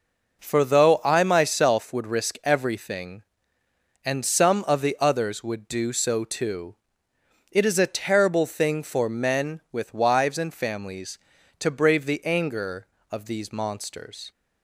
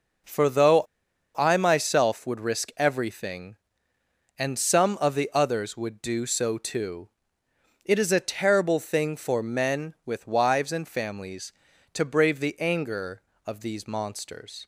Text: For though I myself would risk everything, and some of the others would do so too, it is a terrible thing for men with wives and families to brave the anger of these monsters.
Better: first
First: none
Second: pauses between "though" and "I"; noticeable; at 0.8 s; 0.52 s long

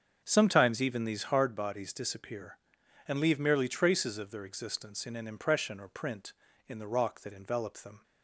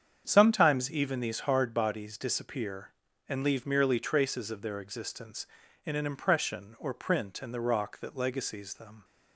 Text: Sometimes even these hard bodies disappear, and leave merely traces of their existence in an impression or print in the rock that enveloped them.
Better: first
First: starts louder than the rest; until 1.2 s; 7 dB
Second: starts louder than the rest; strong; until 1.2 s; 7.5 dB // says "legacies" for "enveloped"; at 8.1 s

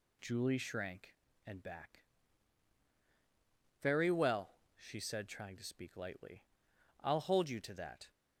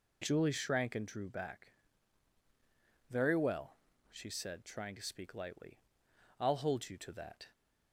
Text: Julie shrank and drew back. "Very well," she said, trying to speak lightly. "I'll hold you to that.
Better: second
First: skips "drew"; at 1.6 s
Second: none

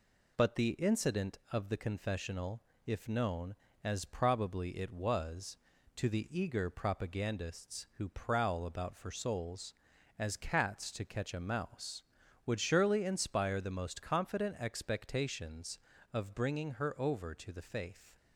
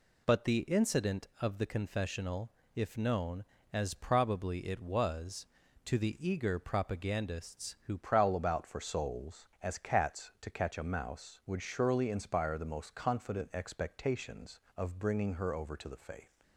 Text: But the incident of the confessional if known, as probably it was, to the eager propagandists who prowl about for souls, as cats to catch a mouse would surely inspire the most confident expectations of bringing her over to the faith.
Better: first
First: pauses between "confessional" and "if"; slight; at 2.6 s; 0.24 s long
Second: pauses between "confessional" and "if"; slight; at 2.5 s; 0.24 s long // changes voice at "prowl"; from 8.0 s on; 8.4 s long

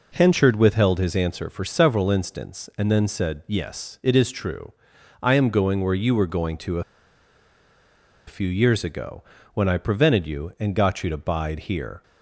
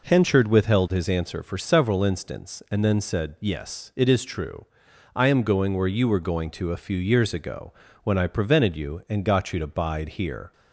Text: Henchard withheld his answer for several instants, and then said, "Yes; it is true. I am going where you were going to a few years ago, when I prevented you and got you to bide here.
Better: second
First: pauses between "a" and "few"; strong; at 6.8 s; 1.4 s long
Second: none

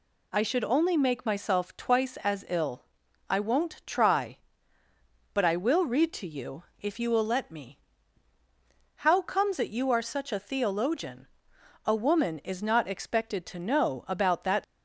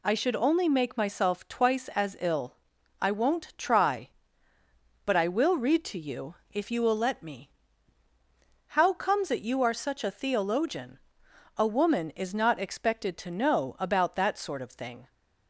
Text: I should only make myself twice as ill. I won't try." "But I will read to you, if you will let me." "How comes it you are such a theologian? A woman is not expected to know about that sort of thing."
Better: second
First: stops before "sort of thing"; at 14.6 s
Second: none

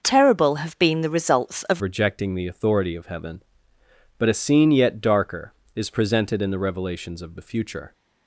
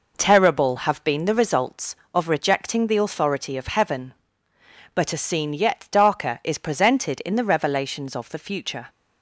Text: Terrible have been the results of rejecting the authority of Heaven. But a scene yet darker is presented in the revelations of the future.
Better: second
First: starts louder than the rest; until 1.0 s; 6 dB // changes voice at "rejecting"; from 1.8 s on; 6.1 s long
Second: none

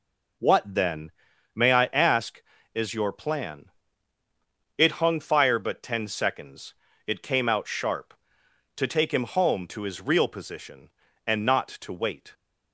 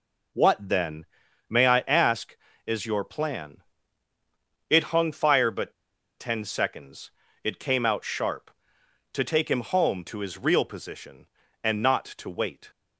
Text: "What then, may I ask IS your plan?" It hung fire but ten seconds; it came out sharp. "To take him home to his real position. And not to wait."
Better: first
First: none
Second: pauses between "but" and "ten"; noticeable; at 5.7 s; 0.46 s long

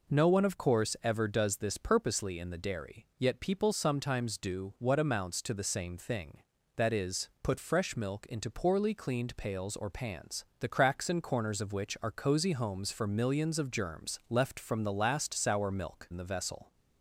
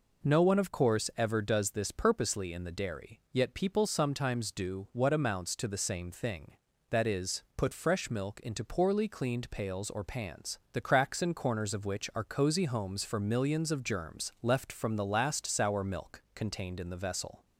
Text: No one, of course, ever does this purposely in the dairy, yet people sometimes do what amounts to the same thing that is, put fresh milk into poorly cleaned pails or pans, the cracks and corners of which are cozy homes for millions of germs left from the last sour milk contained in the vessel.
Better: second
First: skips "contained"; at 16.0 s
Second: none

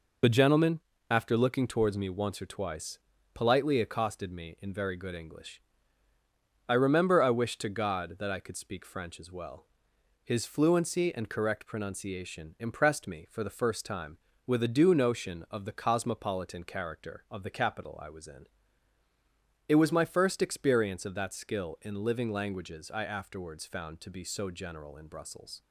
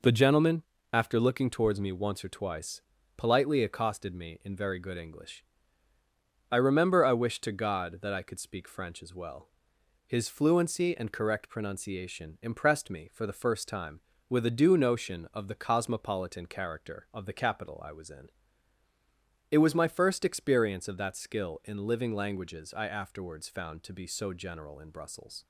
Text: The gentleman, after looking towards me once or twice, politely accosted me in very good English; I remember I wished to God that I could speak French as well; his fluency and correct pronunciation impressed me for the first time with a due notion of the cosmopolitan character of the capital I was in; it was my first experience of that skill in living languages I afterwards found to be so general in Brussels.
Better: second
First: loses the start of "The"; at 0.2 s; 35 ms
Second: none

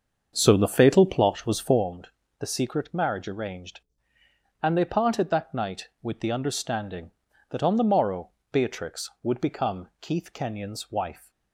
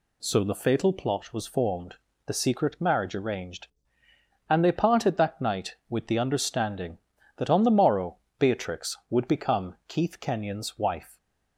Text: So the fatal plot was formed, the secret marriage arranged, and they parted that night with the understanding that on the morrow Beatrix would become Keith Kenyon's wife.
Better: second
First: starts louder than the rest; until 1.9 s; 7 dB // pauses between "morrow" and "Beatrix"; slight; at 8.2 s; 0.20 s long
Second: pauses between "morrow" and "Beatrix"; slight; at 8.1 s; 0.20 s long

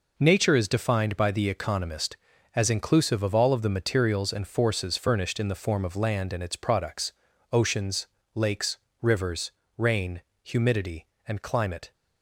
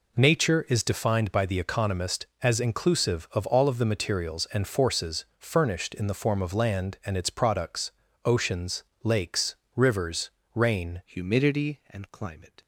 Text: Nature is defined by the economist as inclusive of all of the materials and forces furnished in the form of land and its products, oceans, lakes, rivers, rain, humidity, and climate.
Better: first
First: none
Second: changes voice at "humidity"; from 11.0 s on; 1.6 s long

